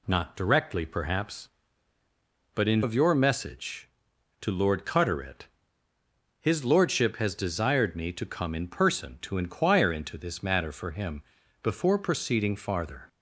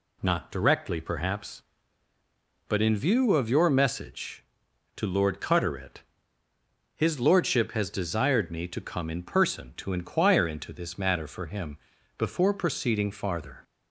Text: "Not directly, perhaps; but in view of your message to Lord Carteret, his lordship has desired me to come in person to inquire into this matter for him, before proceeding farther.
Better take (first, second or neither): second